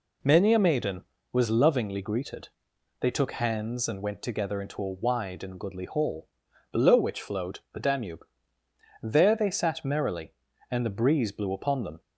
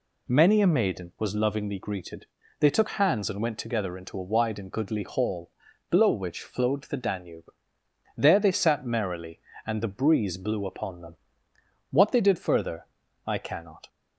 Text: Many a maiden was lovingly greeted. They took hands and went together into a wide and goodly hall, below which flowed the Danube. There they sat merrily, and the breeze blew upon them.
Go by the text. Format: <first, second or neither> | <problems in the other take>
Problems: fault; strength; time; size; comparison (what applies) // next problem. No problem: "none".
first | goes on to say "What they did further I cannot"; strong; from 11.8 s on; 1.9 s long